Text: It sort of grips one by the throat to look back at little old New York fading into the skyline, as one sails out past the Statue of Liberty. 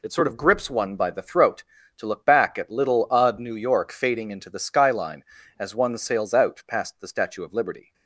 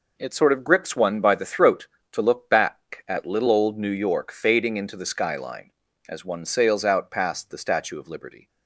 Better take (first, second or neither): second